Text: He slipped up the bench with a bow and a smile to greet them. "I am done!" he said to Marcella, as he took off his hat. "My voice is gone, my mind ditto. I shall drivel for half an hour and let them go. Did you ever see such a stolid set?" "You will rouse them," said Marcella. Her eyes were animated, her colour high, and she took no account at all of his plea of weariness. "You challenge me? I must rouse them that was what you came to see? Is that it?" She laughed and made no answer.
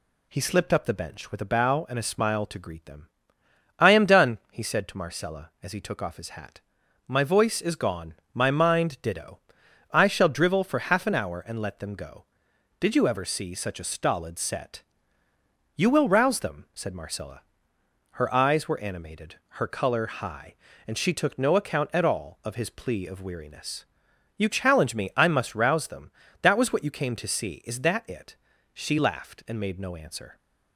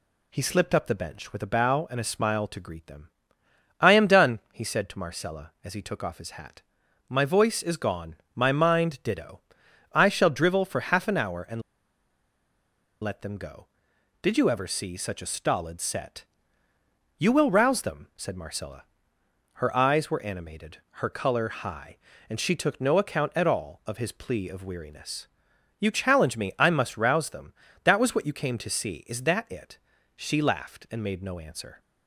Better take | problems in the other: first | pauses between "and" and "let"; strong; at 11.6 s; 1.4 s long

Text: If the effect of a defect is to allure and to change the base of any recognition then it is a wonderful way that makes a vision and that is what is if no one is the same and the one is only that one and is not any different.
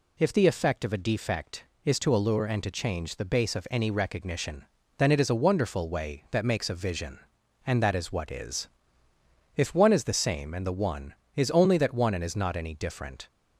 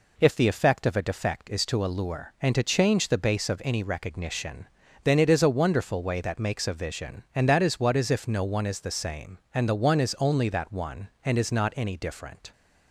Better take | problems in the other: second | pauses between "recognition" and "then"; slight; at 4.6 s; 0.32 s long; slight in the second // pauses between "is" and "if"; noticeable; at 8.6 s; 0.88 s long // skips "no"; at 9.7 s

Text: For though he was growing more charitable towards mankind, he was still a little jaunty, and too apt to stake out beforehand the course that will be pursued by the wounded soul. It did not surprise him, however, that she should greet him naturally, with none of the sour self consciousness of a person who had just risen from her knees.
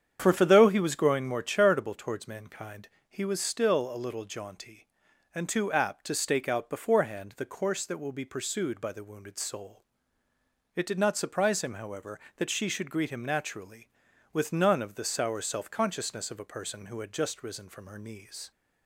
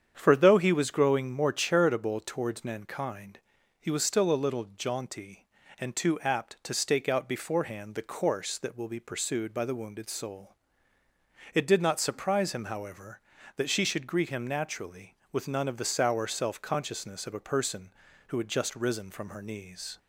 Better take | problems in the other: second | starts louder than the rest; strong; until 1.2 s; 8 dB; strong in the second // says "For" twice; at 0.3 s

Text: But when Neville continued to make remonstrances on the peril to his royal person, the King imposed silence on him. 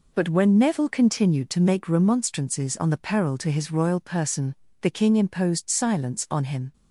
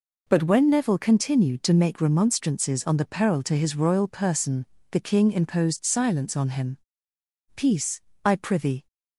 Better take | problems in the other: first | goes on to say "Peace I prithee"; from 7.5 s on; 1.3 s long

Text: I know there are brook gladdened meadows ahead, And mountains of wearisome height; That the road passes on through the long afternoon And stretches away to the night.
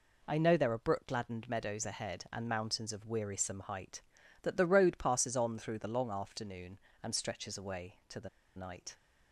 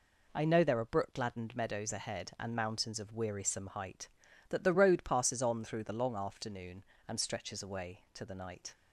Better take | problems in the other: second | pauses between "the" and "night"; slight; at 8.2 s; 0.28 s long

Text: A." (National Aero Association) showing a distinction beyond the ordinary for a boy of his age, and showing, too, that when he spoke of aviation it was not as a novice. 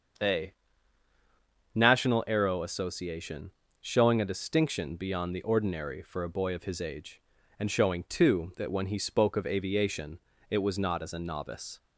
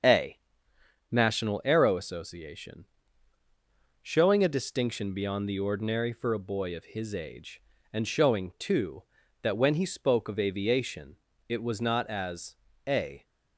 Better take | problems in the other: first | starts louder than the rest; until 1.8 s; 7 dB; strong in the first // pauses between "aviation" and "it"; slight; at 11.1 s; 0.32 s long; slight in the first // pauses between "as" and "a"; slight; at 12.5 s; 0.32 s long // stops before "novice"; at 13.2 s

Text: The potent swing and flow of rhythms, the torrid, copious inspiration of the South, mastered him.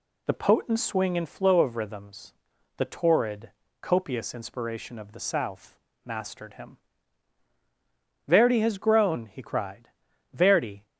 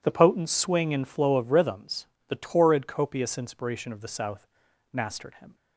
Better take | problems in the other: second | goes on to say "Verdi has grown he cried Verdi"; strong; from 8.2 s on; 2.5 s long

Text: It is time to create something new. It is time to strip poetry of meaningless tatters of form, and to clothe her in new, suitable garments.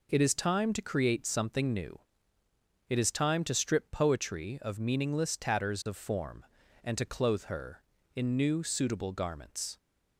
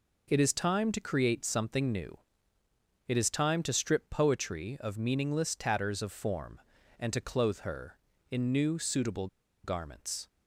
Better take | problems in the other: first | pauses between "suitable" and "garments"; at 9.2 s; 0.37 s long

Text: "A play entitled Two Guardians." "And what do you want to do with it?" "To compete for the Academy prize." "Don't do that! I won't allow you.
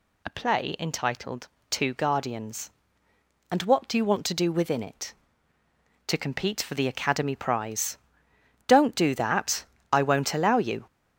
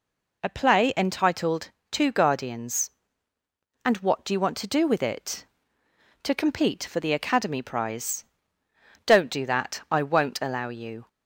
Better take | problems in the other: second | pauses between "entitled" and "Two"; slight; at 1.4 s; 0.24 s long; slight in the second // says "within" for "with"; at 4.5 s

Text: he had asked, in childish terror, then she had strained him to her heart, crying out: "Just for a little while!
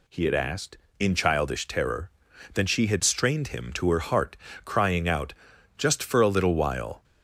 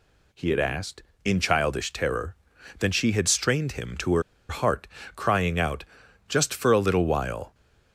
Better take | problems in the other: first | pauses between "her" and "heart"; slight; at 4.2 s; 0.27 s long

